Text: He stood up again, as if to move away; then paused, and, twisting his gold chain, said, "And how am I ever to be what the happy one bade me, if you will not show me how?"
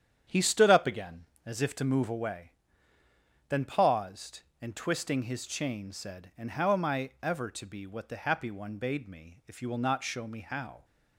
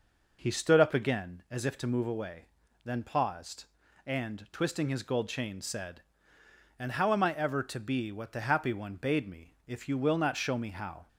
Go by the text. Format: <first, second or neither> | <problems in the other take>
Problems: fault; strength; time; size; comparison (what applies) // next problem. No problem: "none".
second | starts louder than the rest; strong; until 1.5 s; 9 dB // skips "gold"; at 5.4 s